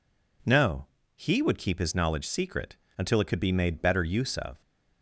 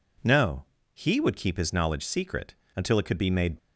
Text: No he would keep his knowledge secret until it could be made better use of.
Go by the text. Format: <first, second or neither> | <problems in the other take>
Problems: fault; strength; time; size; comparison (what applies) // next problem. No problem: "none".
first | pauses between "No" and "he"; slight; at 0.6 s; 0.28 s long; slight in the first // pauses between "secret" and "until"; slight; at 2.5 s; 0.20 s long; slight in the first // stops before "better use of"; at 3.5 s